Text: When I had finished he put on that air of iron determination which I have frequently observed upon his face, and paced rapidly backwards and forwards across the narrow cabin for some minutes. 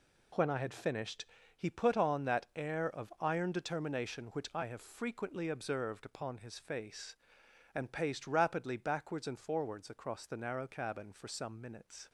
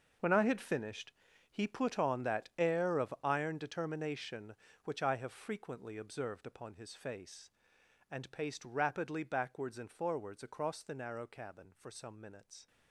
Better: first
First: pauses between "finished" and "he"; slight; at 1.2 s; 0.30 s long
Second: gets quieter; strong; throughout; 14 dB // pauses between "finished" and "he"; at 1.1 s; 0.38 s long

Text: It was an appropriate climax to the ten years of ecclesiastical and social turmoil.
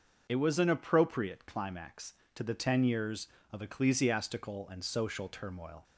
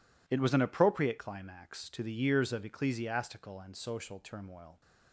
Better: first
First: none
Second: skips "ten"; at 2.1 s

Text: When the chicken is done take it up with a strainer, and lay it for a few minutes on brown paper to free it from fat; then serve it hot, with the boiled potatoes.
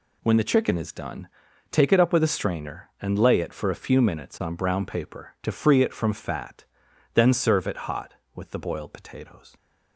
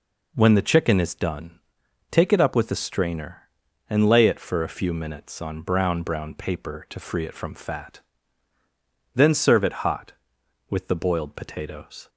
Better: first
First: pauses between "done" and "take"; at 1.2 s; 0.44 s long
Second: pauses between "done" and "take"; noticeable; at 1.5 s; 0.52 s long // says "brown" twice; at 6.0 s

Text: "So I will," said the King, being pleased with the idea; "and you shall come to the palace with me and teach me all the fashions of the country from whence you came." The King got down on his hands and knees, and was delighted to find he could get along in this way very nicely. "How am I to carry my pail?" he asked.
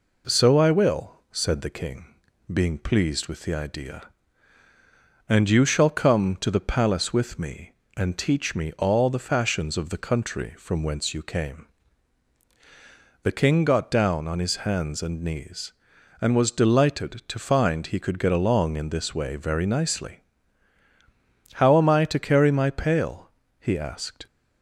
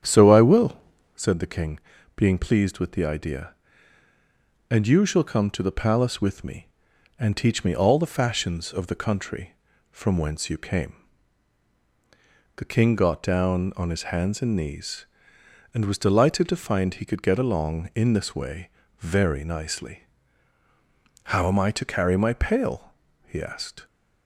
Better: first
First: none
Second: starts louder than the rest; strong; until 1.2 s; 9 dB // pauses between "way" and "very"; slight; at 18.6 s; 0.30 s long

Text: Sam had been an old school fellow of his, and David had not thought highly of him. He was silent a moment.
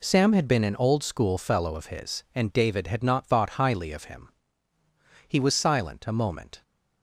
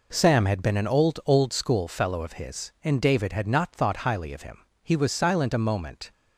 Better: first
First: none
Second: says "old" twice; at 1.2 s

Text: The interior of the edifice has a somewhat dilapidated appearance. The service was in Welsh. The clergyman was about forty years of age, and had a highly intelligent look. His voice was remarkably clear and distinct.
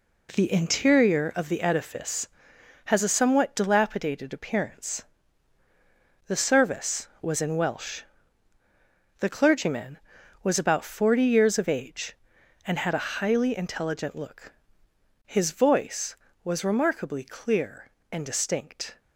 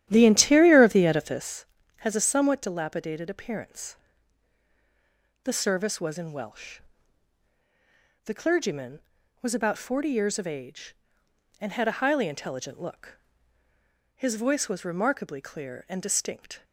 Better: first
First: none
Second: starts louder than the rest; strong; until 1.5 s; 11.5 dB

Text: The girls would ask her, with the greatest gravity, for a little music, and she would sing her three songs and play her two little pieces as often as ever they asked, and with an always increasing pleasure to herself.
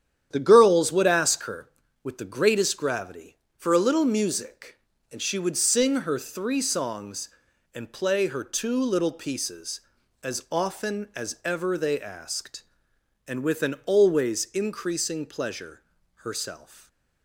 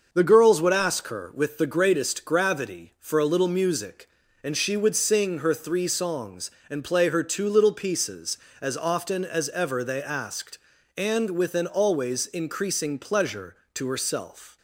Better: second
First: starts louder than the rest; strong; until 1.3 s; 9.5 dB // skips "to"; at 16.0 s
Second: starts louder than the rest; until 1.1 s; 6 dB

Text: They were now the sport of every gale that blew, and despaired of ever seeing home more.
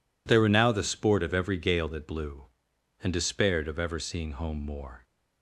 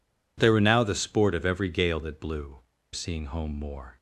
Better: first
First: none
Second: skips "and despaired of ever"; at 2.7 s

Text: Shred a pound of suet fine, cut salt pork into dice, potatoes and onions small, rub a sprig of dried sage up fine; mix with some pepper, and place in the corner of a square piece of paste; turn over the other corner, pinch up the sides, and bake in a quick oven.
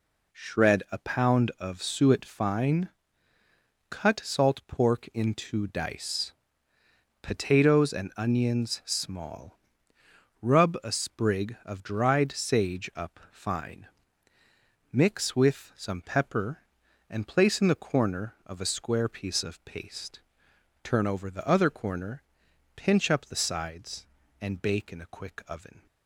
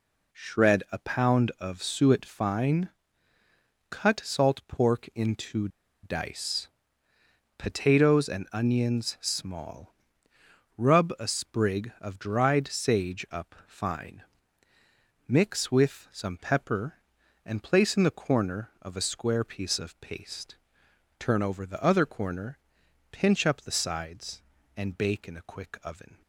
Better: first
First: none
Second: pauses between "into" and "dice"; slight; at 5.6 s; 0.34 s long

